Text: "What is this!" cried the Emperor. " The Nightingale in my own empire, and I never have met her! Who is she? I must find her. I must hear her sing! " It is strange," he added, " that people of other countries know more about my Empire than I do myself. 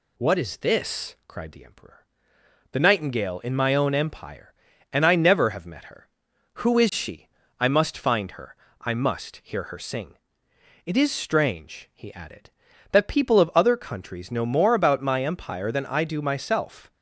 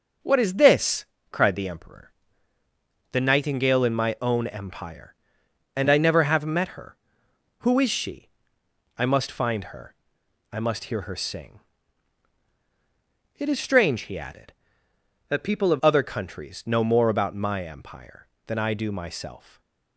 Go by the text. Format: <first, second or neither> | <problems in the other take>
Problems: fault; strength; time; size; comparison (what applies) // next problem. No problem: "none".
first | starts louder than the rest; until 1.4 s; 6.5 dB // changes voice from "that" to "of"; from 15.2 to 15.7 s; 0.5 s long // stays silent after the last word; slight; from 19.3 s on; 0.6 s long